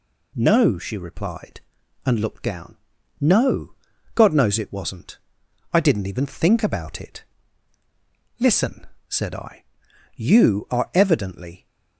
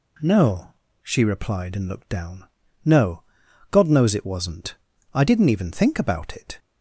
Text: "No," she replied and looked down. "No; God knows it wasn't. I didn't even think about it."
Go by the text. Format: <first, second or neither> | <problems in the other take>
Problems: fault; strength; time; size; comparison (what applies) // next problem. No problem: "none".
second | goes on to say "Listen said I you are evidently"; strong; from 8.4 s on; 3.2 s long